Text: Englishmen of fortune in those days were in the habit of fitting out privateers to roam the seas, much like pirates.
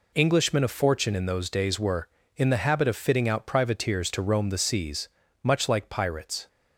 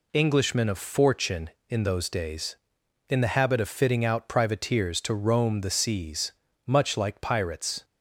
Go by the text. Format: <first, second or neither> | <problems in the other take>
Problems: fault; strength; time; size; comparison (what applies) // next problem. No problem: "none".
first | skips "were"; at 2.8 s